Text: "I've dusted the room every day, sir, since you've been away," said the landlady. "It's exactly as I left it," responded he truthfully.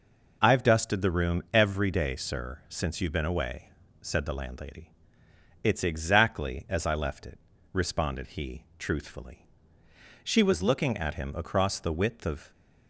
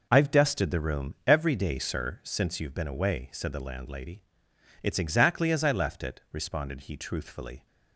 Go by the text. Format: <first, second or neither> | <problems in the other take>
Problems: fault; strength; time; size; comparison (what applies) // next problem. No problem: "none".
second | goes on to say "She was looking at him across the width of"; strong; from 10.2 s on; 2.2 s long